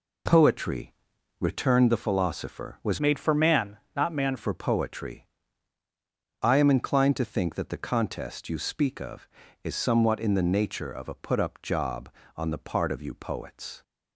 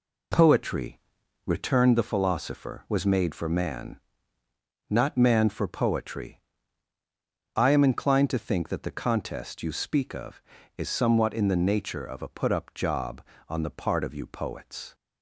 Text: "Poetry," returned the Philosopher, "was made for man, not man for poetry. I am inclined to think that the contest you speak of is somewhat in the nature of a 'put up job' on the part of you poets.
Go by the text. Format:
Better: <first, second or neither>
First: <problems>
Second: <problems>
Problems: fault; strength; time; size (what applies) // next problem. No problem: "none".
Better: second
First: changes voice from "made" to "man"; from 2.9 to 4.3 s; 1.4 s long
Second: none